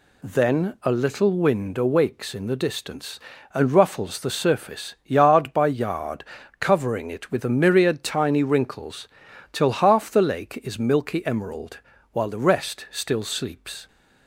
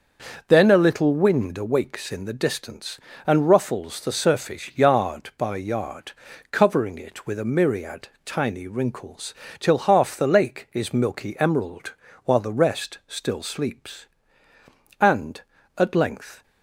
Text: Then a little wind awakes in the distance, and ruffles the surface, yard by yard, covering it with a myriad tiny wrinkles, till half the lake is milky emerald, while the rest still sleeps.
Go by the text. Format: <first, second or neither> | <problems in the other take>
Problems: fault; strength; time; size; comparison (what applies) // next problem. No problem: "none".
first | starts louder than the rest; until 1.4 s; 6.5 dB // pauses between "myriad" and "tiny"; slight; at 8.0 s; 0.16 s long // goes on to say "And at length"; from 14.9 s on; 1.4 s long